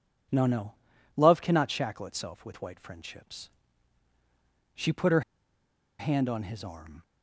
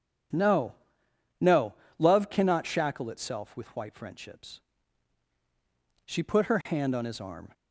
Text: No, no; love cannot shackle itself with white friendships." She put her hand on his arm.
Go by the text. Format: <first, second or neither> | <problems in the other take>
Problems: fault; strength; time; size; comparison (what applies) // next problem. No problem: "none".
second | pauses between "her" and "hand"; noticeable; at 5.2 s; 0.78 s long